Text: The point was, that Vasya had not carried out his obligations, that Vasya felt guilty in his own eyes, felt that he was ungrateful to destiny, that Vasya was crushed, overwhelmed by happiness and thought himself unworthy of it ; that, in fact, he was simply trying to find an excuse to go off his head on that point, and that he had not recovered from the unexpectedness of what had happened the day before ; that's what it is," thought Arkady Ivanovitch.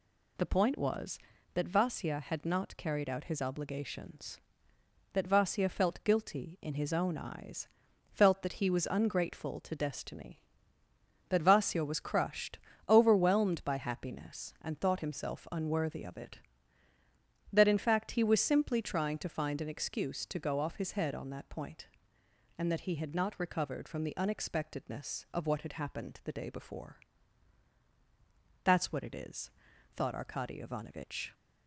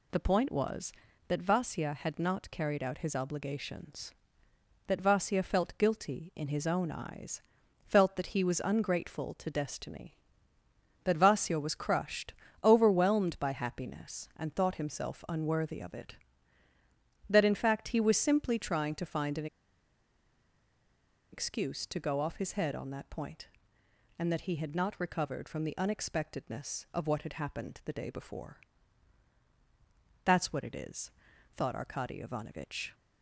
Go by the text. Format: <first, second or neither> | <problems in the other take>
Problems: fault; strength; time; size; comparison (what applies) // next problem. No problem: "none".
first | pauses between "an" and "excuse"; strong; at 19.4 s; 1.8 s long